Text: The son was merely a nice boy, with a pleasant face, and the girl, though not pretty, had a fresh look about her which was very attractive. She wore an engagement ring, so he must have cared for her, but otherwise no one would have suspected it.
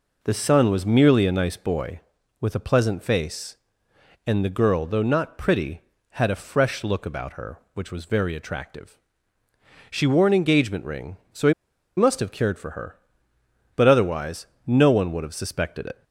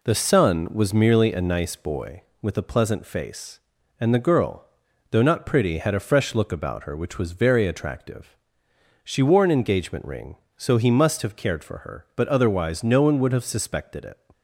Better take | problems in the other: second | pauses between "he" and "must"; at 11.5 s; 0.43 s long // pauses between "otherwise" and "no"; slight; at 14.4 s; 0.18 s long

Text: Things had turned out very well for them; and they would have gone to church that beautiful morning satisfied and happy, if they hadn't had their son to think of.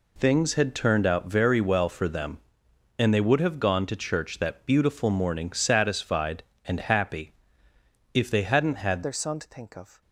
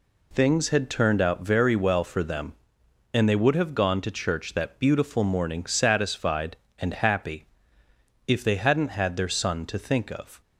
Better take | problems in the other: second | changes voice at "their"; from 9.0 s on; 1.0 s long

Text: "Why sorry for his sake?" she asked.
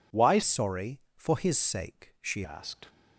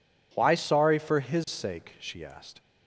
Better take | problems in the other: second | changes voice from "sorry" to "she"; from 0.4 to 2.4 s; 2.0 s long

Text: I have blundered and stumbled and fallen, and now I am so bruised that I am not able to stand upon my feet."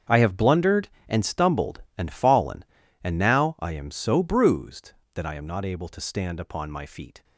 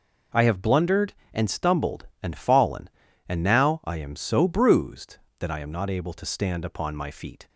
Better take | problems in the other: second | gets quieter; strong; throughout; 15 dB

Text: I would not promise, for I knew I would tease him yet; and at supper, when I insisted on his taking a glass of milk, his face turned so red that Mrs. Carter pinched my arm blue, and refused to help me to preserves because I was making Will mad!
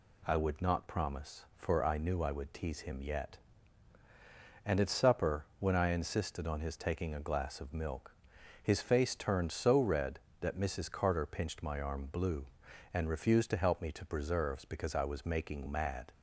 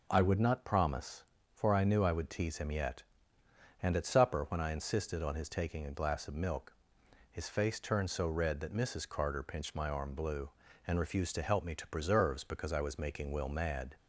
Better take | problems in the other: second | skips "Will"; at 15.6 s

